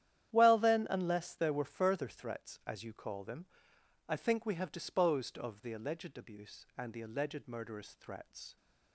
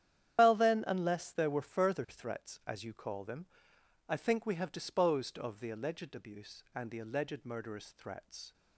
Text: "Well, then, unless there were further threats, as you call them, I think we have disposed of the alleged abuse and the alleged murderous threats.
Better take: first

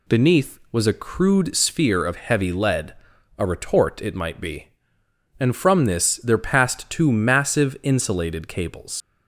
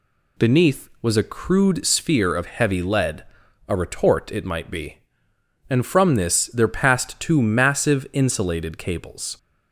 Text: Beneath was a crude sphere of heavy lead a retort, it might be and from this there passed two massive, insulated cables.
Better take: second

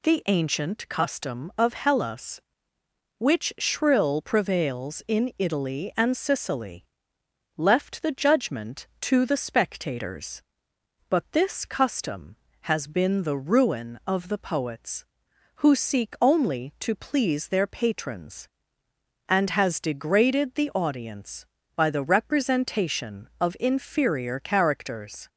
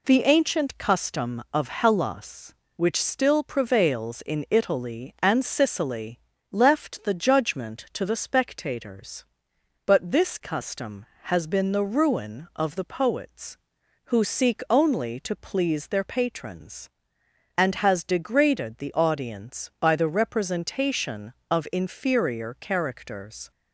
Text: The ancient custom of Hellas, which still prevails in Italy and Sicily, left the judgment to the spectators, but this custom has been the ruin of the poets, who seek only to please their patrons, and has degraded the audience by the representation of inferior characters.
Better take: second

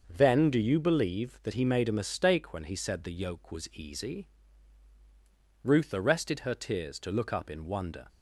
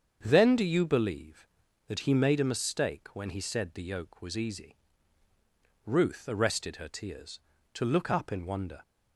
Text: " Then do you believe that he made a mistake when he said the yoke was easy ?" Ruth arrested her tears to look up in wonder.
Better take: neither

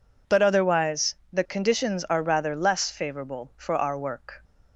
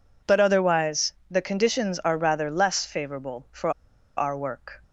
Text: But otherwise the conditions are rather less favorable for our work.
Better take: first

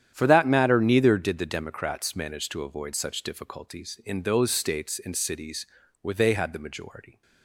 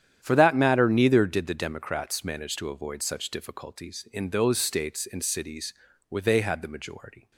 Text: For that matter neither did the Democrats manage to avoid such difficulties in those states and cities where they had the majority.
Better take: neither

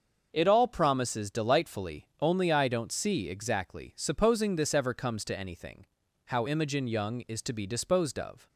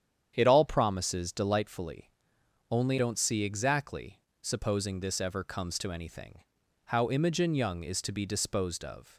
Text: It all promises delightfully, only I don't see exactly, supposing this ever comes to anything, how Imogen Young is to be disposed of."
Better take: first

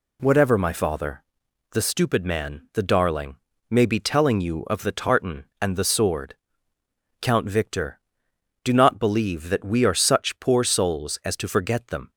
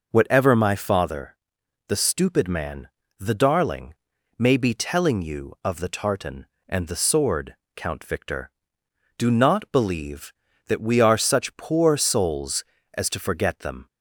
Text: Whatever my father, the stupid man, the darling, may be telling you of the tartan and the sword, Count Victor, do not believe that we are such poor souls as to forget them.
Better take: neither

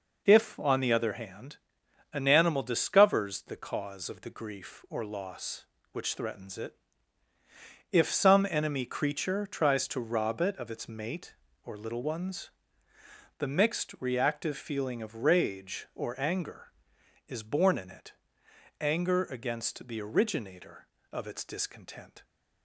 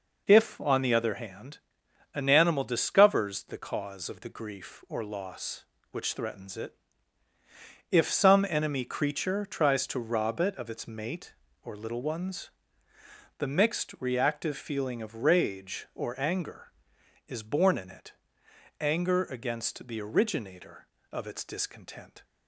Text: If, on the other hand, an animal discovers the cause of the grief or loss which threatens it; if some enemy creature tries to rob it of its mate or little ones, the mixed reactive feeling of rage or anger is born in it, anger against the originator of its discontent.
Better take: neither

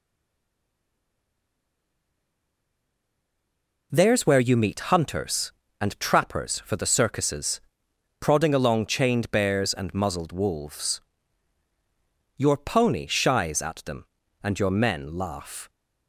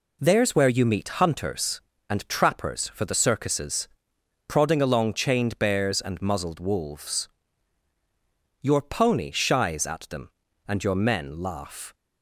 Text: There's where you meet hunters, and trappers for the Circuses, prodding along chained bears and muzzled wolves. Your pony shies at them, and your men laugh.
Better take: second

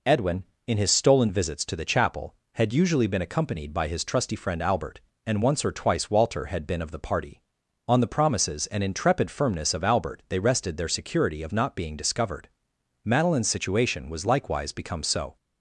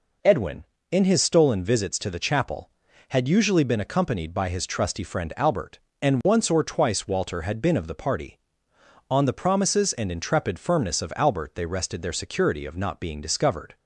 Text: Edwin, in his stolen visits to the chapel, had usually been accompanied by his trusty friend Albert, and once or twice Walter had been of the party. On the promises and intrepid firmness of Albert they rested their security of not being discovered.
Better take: second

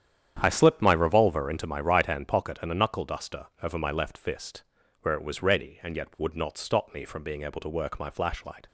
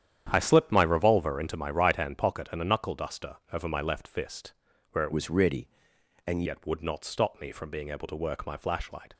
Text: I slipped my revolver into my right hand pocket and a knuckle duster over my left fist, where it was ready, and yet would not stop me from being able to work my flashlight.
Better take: first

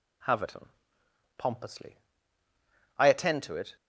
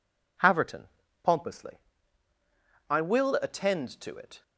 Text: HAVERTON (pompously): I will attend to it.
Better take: second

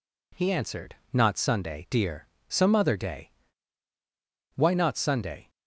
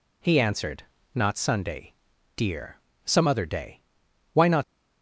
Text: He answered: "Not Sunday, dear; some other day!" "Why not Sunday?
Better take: first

